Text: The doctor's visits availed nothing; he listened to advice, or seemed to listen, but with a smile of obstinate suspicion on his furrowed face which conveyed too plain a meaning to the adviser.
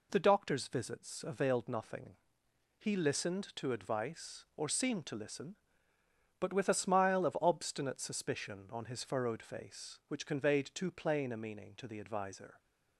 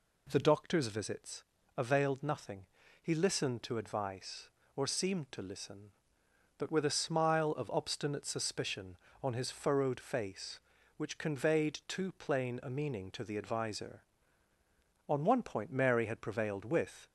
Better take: first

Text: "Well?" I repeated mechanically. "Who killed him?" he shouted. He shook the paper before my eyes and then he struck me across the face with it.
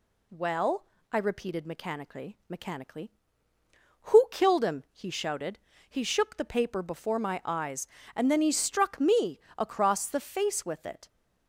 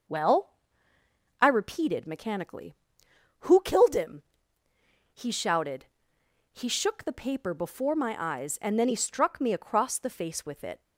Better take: second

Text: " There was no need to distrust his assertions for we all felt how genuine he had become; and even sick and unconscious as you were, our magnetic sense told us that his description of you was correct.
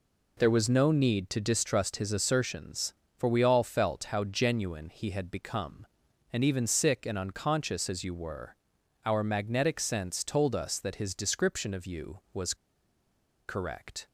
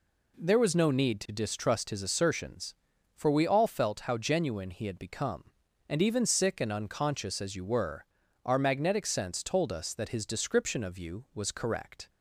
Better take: second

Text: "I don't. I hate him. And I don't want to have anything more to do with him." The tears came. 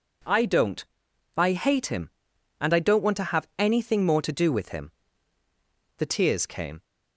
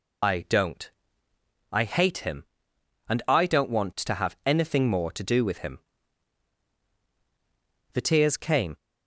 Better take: first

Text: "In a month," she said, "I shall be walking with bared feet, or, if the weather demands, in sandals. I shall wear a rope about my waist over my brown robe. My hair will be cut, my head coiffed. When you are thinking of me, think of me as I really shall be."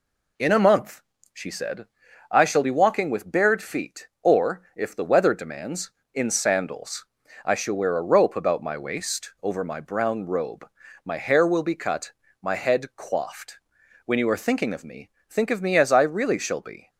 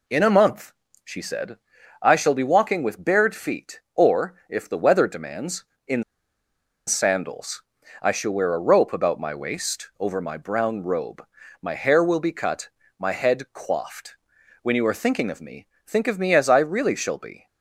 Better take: first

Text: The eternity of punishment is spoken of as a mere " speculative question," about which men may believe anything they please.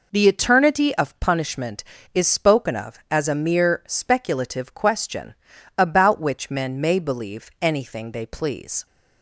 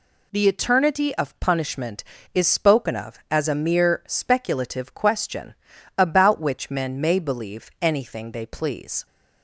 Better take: second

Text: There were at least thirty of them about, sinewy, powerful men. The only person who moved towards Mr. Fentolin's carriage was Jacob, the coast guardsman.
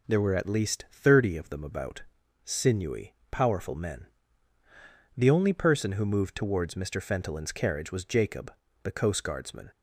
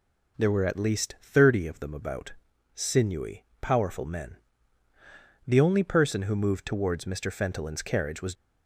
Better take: first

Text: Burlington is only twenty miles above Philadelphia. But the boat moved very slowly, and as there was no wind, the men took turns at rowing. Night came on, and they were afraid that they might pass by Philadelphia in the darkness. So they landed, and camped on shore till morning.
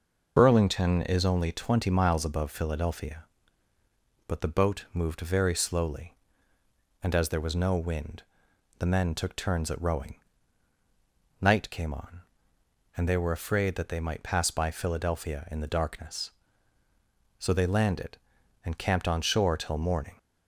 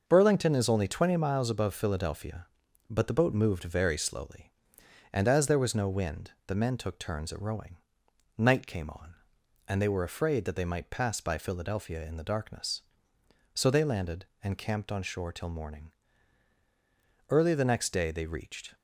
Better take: first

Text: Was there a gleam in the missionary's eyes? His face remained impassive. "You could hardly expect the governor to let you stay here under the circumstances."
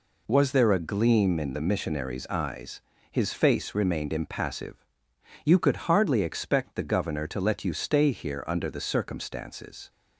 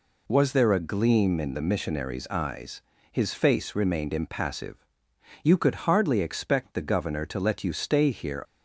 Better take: first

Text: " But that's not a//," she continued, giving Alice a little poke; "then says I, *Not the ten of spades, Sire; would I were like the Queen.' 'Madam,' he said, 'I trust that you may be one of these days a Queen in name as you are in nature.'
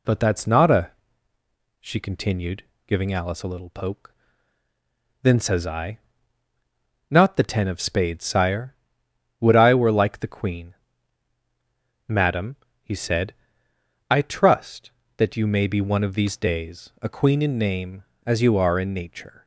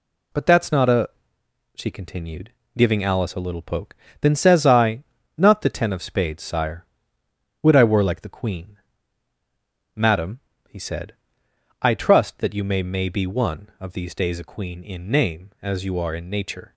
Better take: first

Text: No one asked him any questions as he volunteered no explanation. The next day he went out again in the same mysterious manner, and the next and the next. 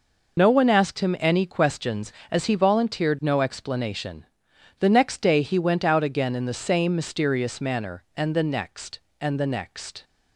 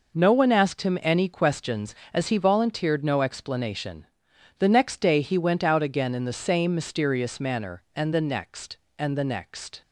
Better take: second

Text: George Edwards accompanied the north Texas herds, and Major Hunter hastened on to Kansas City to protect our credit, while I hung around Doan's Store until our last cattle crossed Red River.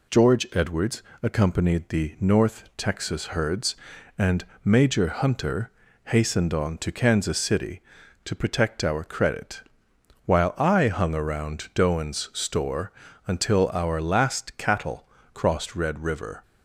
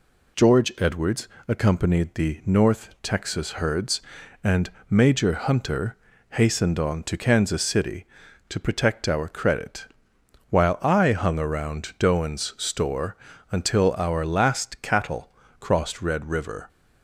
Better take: neither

